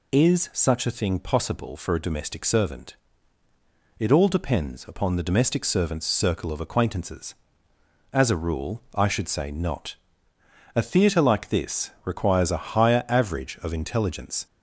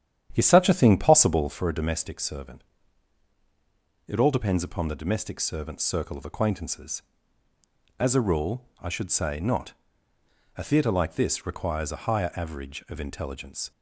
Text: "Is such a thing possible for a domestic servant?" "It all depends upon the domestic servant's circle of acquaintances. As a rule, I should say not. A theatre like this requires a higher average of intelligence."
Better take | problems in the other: first | starts louder than the rest; strong; until 1.6 s; 9.5 dB

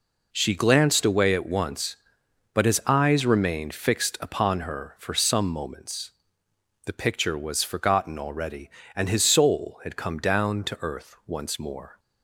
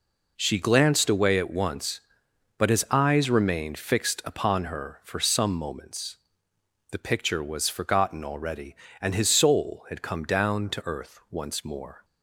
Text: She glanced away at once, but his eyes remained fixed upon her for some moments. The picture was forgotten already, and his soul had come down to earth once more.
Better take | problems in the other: neither | none

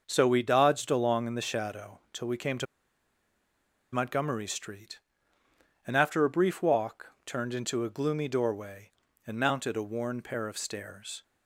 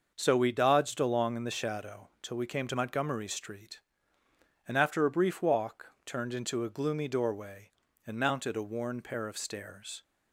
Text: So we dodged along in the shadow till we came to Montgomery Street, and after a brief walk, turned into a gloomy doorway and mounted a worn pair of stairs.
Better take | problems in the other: second | pauses between "to" and "Montgomery"; strong; at 2.6 s; 1.2 s long

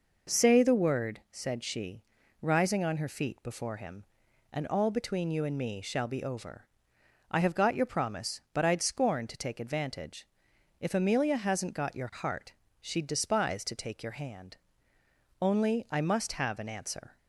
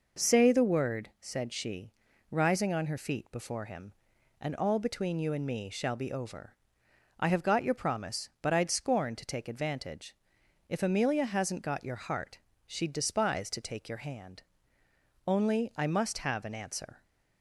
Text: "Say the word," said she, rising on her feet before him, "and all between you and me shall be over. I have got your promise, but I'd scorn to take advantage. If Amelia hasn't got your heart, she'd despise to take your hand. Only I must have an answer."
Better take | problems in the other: neither | none

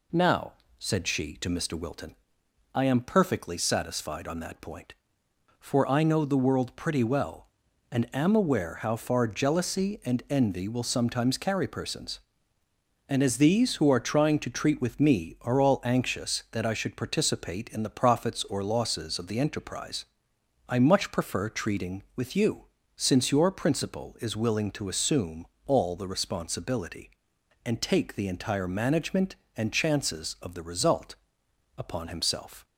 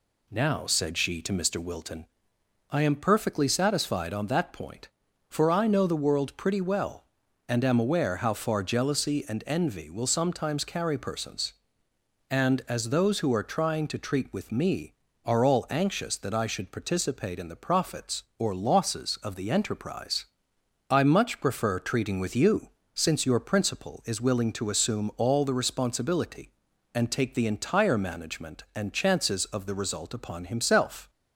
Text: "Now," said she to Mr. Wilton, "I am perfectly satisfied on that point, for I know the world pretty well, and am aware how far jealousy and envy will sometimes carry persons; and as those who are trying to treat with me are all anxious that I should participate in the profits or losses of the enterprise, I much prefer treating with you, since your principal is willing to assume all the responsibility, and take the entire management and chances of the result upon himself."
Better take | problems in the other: second | says "these" for "those"; at 13.3 s // pauses between "assume" and "all"; slight; at 25.4 s; 0.20 s long // pauses between "result" and "upon"; noticeable; at 31.1 s; 0.60 s long

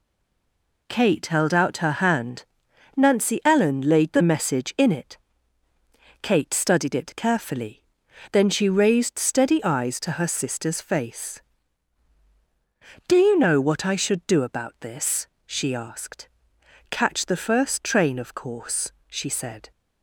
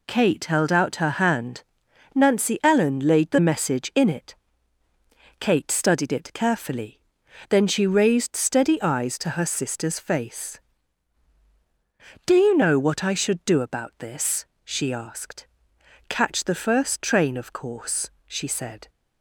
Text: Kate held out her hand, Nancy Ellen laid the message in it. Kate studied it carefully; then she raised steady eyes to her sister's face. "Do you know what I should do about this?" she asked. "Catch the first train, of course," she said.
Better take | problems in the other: second | stays silent before the first word; slight; until 0.8 s; 0.8 s long

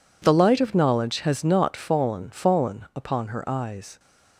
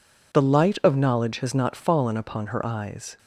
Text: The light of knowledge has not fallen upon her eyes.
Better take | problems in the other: second | says "fallen" twice; at 2.2 s

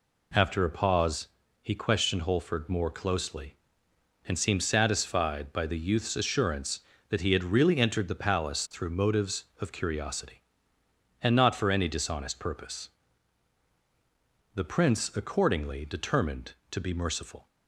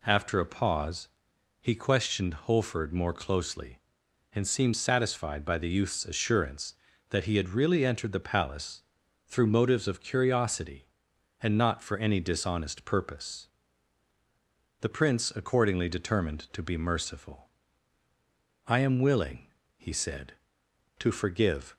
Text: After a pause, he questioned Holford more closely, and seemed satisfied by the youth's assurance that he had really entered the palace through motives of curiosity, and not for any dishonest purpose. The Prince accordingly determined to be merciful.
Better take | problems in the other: first | pauses between "palace" and "through"; at 8.8 s; 0.44 s long // goes on to say "I am willing he said to forgive"; strong; from 18.6 s on; 3.1 s long

